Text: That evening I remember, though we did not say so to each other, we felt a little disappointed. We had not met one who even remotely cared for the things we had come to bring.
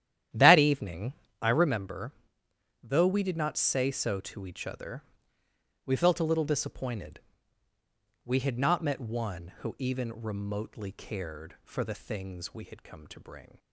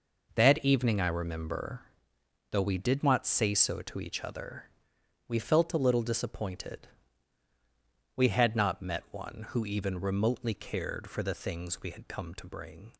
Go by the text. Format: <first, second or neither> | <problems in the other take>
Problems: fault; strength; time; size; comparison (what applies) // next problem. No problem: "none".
second | starts louder than the rest; strong; until 1.8 s; 11 dB // pauses between "evening" and "I"; slight; at 1.1 s; 0.28 s long